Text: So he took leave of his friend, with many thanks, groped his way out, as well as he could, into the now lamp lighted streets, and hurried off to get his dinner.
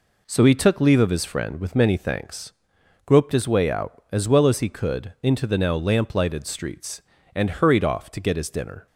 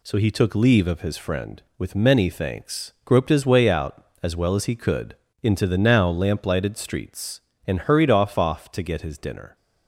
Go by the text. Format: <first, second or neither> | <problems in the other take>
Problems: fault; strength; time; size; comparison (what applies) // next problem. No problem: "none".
first | says "off" twice; at 8.3 s